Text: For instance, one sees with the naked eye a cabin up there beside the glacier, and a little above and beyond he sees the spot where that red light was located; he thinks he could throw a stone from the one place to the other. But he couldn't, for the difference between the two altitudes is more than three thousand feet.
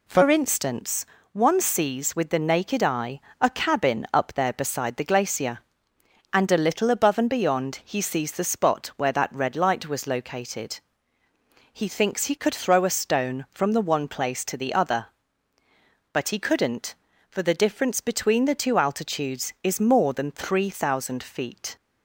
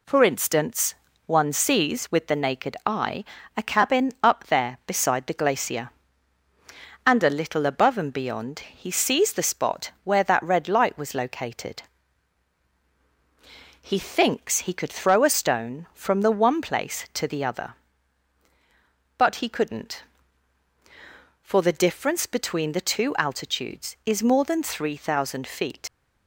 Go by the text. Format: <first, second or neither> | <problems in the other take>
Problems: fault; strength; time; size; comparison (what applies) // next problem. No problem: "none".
first | pauses between "eye" and "a"; slight; at 3.2 s; 0.32 s long; slight in the first // leaves "feet" unfinished; at 25.8 s; 85 ms